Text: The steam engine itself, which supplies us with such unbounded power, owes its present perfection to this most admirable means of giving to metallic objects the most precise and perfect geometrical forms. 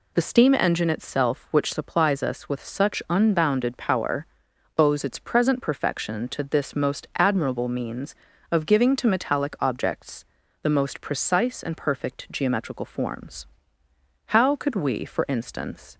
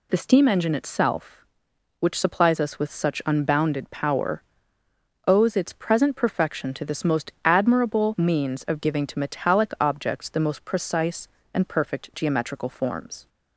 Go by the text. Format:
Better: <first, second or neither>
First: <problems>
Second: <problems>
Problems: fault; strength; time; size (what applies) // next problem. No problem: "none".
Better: second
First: pauses between "objects" and "the"; at 10.2 s; 0.38 s long // goes on to say "How could we for instance"; strong; from 14.2 s on; 1.7 s long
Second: none